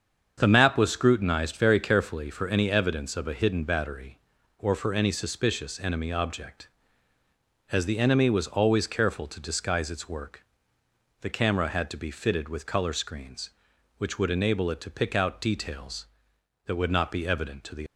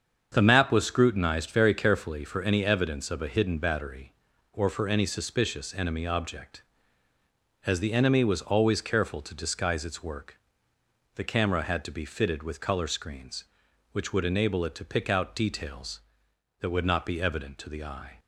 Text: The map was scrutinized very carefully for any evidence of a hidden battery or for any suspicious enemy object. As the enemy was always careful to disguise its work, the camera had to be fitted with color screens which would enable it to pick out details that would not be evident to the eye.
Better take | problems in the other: second | starts louder than the rest; until 1.3 s; 7 dB; also in the second // stops before "eye"; at 17.8 s

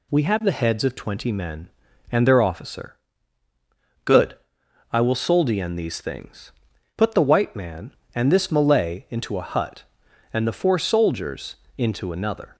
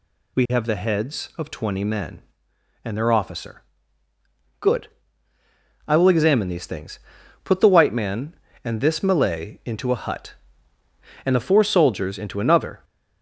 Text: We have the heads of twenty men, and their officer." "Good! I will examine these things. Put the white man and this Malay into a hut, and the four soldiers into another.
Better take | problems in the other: second | says "soldien" for "examine"; at 5.1 s // pauses between "soldiers" and "into"; slight; at 11.5 s; 0.20 s long

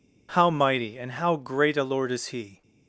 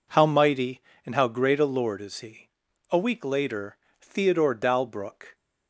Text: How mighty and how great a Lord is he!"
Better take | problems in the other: first | goes on to say "A week later Theodore Dalbrook"; strong; from 2.8 s on; 2.4 s long

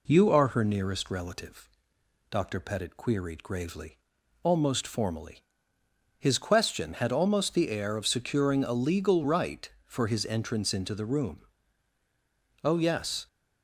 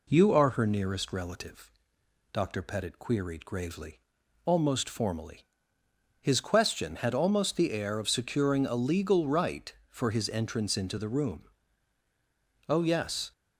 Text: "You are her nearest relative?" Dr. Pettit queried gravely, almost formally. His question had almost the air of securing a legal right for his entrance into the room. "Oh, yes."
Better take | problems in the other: neither | none

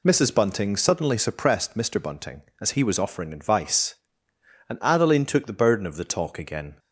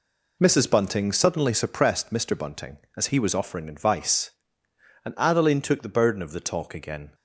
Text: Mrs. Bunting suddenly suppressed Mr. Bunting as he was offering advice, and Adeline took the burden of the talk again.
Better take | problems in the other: first | gets quieter; strong; throughout; 8.5 dB

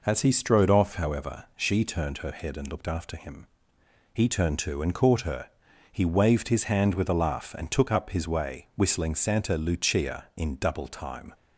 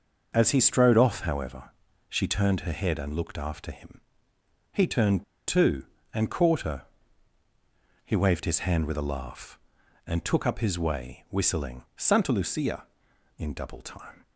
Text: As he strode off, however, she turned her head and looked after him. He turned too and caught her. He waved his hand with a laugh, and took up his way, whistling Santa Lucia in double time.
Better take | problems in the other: first | starts louder than the rest; noticeable; until 1.3 s; 6 dB // pauses between "turned" and "too"; slight; at 5.2 s; 0.25 s long

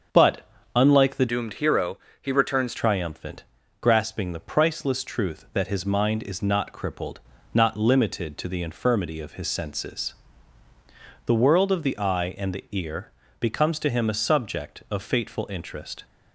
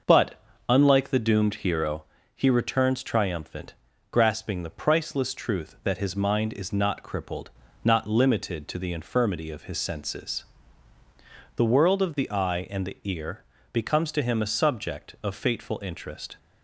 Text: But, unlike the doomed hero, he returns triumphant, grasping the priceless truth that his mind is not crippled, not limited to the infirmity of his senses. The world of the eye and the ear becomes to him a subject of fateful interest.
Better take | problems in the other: second | starts louder than the rest; until 1.3 s; 7 dB // changes voice from "doomed" to "returns"; from 1.2 to 2.7 s; 1.5 s long // pauses between "ear" and "becomes"; slight; at 13.1 s; 0.28 s long; slight in the second

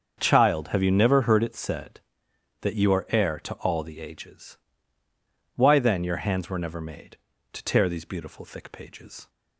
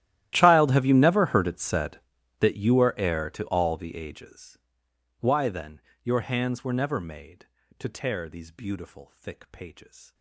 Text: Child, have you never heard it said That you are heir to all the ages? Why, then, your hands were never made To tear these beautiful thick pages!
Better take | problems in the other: first | gets quieter; strong; throughout; 25.5 dB // starts louder than the rest; strong; until 1.3 s; 13 dB; also in the first

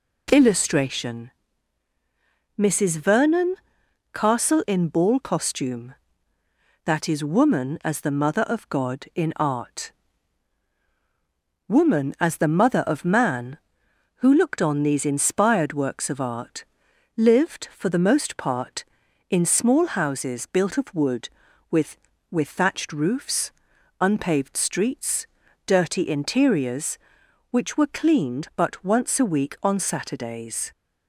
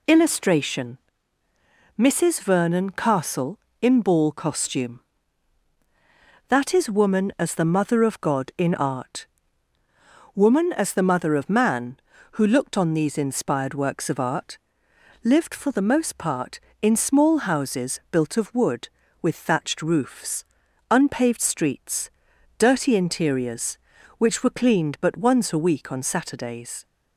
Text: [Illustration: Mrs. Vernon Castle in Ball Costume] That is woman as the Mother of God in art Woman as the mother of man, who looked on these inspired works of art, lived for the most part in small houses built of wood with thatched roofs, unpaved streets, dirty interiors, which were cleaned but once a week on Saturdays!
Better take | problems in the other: second | pauses between "Vernon" and "Castle"; noticeable; at 3.5 s; 0.58 s long // pauses between "art" and "Woman"; strong; at 9.9 s; 1.7 s long; also in the second // says "with" twice; at 22.2 s

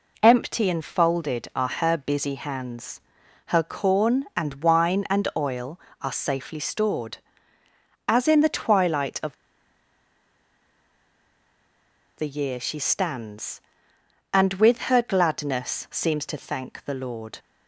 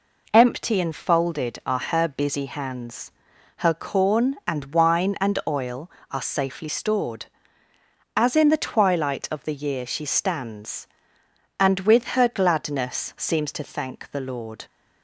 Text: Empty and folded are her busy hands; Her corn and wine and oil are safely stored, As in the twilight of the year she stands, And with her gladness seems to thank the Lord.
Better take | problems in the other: second | pauses between "of" and "the"; strong; at 9.3 s; 2.8 s long

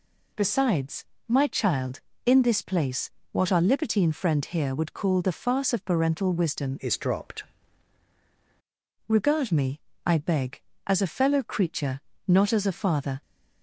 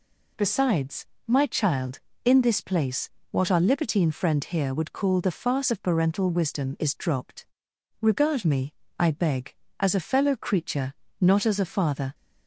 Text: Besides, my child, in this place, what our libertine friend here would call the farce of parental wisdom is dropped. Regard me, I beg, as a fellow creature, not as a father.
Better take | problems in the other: second | changes voice from "is" to "dropped"; from 6.7 to 7.4 s; 0.7 s long

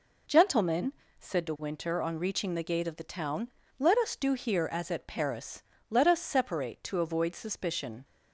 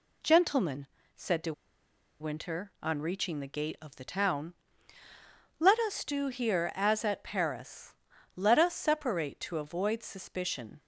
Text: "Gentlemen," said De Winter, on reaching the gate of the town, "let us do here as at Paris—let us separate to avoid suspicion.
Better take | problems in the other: first | pauses between "De" and "Winter"; noticeable; at 1.5 s; 0.68 s long

